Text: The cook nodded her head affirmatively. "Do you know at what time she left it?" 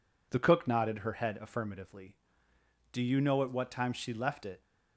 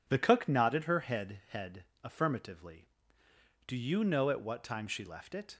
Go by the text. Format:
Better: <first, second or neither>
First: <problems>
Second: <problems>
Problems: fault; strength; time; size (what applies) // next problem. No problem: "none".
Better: first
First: none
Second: says "head" twice; at 1.4 s